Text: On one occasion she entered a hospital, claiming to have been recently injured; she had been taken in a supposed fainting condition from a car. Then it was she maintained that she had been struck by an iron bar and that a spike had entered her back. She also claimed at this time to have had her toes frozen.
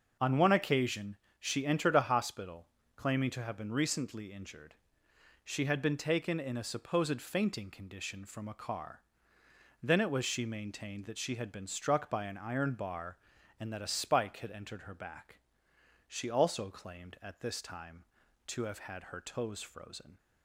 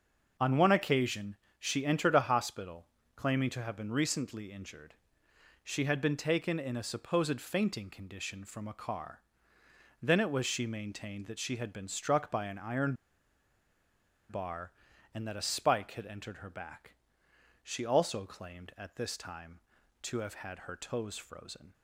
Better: first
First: starts louder than the rest; until 1.4 s; 6.5 dB // pauses between "occasion" and "she"; slight; at 1.1 s; 0.22 s long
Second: starts louder than the rest; until 1.6 s; 6.5 dB // pauses between "occasion" and "she"; slight; at 1.3 s; 0.22 s long // pauses between "iron" and "bar"; strong; at 12.9 s; 1.3 s long

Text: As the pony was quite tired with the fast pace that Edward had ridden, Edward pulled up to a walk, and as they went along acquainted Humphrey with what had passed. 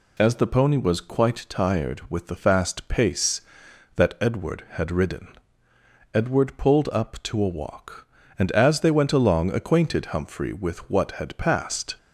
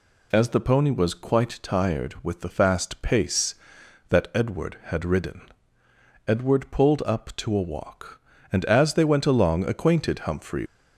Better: first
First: none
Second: stops before "with what had passed"; at 10.6 s

